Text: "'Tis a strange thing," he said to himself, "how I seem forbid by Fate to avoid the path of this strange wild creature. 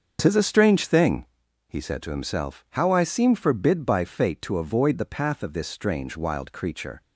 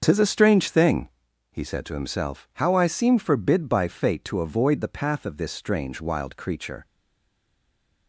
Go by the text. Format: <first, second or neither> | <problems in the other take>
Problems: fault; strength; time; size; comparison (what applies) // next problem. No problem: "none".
first | starts louder than the rest; until 1.0 s; 7 dB; also in the first // stays silent after the last word; noticeable; from 6.8 s on; 1.2 s long